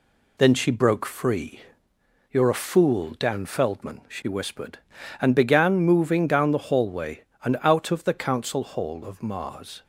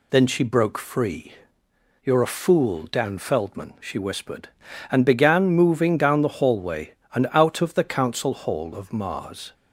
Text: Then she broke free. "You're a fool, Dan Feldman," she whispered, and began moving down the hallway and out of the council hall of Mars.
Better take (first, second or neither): second